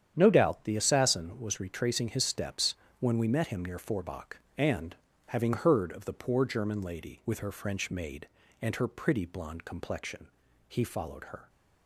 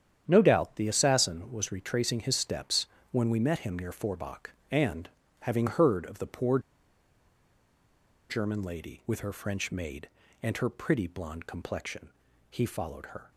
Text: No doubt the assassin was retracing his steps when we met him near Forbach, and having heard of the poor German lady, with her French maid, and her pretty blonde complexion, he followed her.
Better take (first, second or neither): first